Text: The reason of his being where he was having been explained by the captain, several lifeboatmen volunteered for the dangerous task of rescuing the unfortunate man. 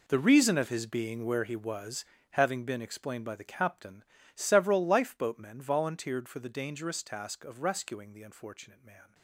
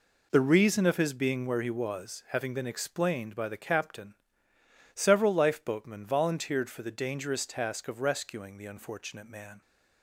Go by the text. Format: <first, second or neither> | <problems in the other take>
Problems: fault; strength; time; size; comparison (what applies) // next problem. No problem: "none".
second | gets quieter; strong; throughout; 15 dB // pauses between "was" and "having"; slight; at 2.0 s; 0.26 s long